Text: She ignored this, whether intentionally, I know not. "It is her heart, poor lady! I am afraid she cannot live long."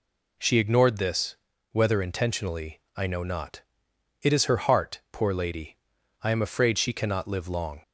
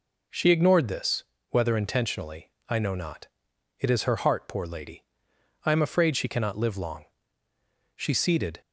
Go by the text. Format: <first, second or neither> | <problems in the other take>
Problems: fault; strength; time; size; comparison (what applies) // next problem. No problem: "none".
first | goes on to say "She seated"; noticeable; from 7.9 s on; 0.64 s long